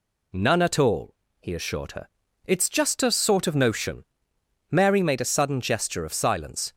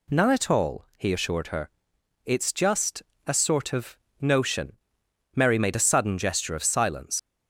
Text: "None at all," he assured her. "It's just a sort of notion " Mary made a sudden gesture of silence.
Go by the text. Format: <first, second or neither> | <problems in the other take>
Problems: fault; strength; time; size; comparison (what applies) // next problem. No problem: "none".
first | pauses between "just" and "a"; slight; at 3.0 s; 0.24 s long // pauses between "of" and "notion"; slight; at 3.9 s; 0.20 s long // leaves "silence" unfinished; at 7.1 s; 75 ms